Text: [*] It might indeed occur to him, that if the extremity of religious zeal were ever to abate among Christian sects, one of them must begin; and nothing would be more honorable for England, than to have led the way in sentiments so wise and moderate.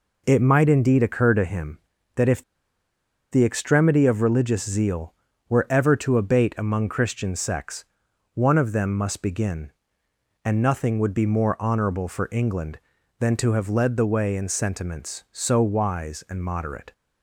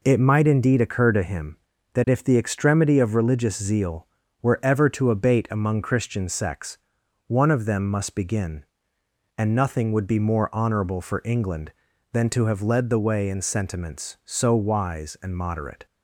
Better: second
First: pauses between "if" and "the"; noticeable; at 2.4 s; 0.88 s long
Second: none

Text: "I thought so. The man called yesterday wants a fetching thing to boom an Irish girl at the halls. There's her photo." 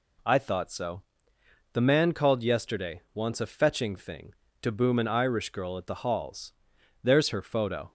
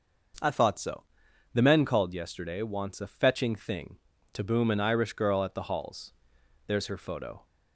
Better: first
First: none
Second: says "men" for "man"; at 1.6 s

